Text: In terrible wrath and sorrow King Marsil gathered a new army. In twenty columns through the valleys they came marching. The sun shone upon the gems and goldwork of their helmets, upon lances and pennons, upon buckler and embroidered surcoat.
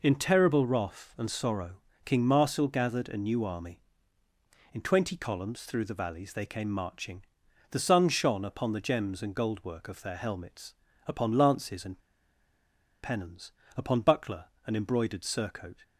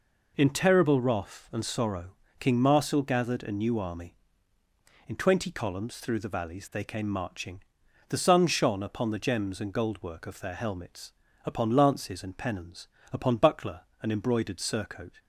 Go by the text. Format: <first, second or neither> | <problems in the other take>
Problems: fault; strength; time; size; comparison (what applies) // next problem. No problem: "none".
second | pauses between "sorrow" and "King"; slight; at 1.7 s; 0.30 s long; slight in the second // pauses between "and" and "pennons"; at 11.9 s; 1.0 s long